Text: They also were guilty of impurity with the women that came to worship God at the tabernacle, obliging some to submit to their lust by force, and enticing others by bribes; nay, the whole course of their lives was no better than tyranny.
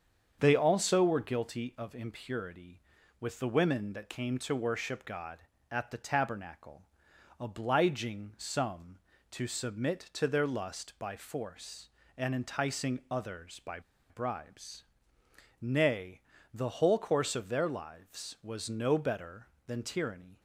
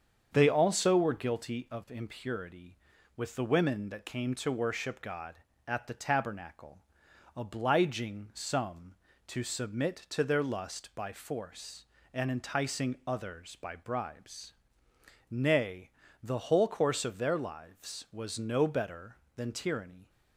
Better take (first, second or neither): second